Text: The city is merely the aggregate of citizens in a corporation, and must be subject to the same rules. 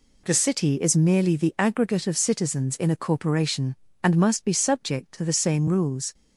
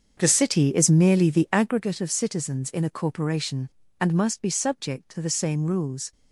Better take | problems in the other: first | starts louder than the rest; until 1.8 s; 7 dB

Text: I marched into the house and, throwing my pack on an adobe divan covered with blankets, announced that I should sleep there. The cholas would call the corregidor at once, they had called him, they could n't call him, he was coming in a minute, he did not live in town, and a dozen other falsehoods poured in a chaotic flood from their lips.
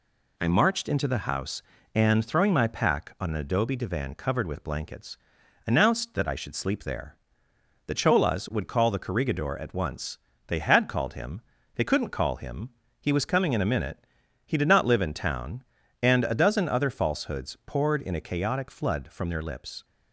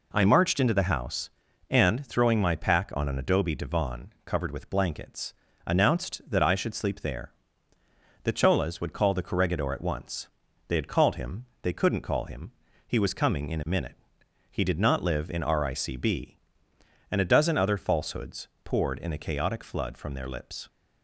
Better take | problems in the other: first | says "ricb" for "town"; at 15.4 s // pauses between "falsehoods" and "poured"; slight; at 18.4 s; 0.16 s long

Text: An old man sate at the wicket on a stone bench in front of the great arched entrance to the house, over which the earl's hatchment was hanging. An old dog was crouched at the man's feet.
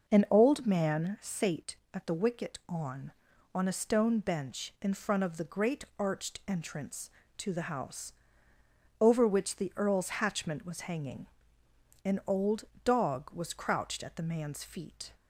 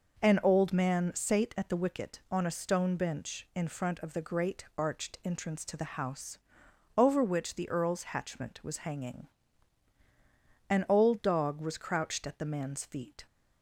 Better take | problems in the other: second | says "on" twice; at 3.5 s // pauses between "great" and "arched"; slight; at 5.8 s; 0.16 s long // pauses between "old" and "dog"; slight; at 12.6 s; 0.20 s long

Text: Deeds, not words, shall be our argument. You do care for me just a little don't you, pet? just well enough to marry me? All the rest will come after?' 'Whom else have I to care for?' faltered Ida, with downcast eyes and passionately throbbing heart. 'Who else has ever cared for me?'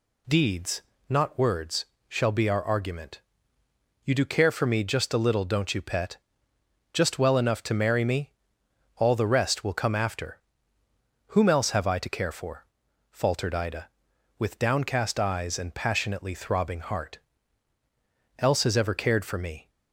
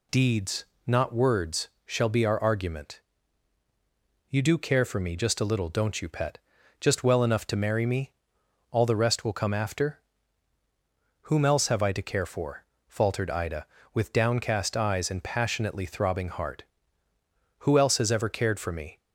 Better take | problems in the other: second | skips "Who"; at 17.7 s

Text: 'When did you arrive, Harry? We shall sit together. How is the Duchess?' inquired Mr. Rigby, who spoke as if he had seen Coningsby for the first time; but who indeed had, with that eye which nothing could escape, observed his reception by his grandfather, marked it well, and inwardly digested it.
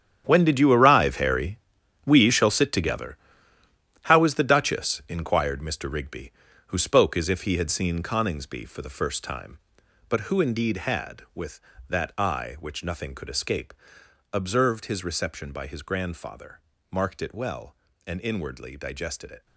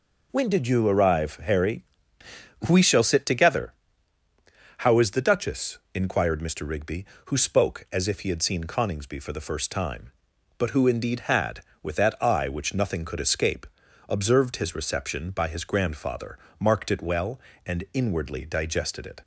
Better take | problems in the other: second | gets quieter; strong; throughout; 13.5 dB

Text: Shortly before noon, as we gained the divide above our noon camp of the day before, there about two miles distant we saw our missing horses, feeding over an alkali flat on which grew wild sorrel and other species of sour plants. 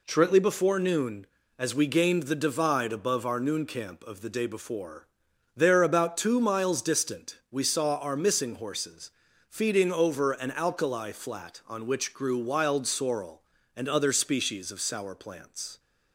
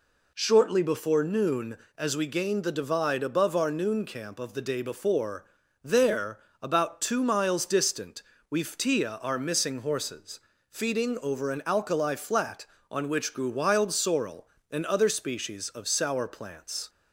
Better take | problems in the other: first | pauses between "there" and "about"; slight; at 6.3 s; 0.20 s long // pauses between "distant" and "we"; slight; at 8.2 s; 0.26 s long // says "ftia" for "saw"; at 8.6 s

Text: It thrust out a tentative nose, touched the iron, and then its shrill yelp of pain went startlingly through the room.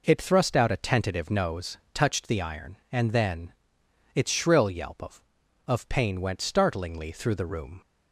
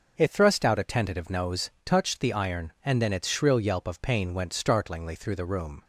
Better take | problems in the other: second | pauses between "then" and "its"; noticeable; at 3.5 s; 0.62 s long // says "of" twice; at 5.6 s

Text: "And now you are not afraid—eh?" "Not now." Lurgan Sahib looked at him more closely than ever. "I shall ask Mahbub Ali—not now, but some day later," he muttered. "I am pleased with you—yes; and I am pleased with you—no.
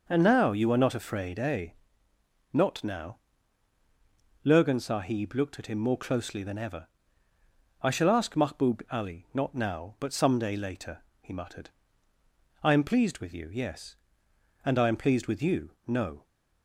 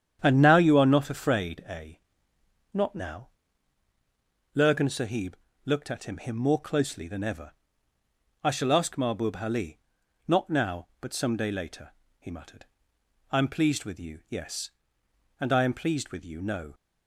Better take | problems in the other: first | starts louder than the rest; strong; until 1.2 s; 9 dB // pauses between "Sahib" and "looked"; slight; at 5.3 s; 0.30 s long // says "him" twice; at 6.1 s

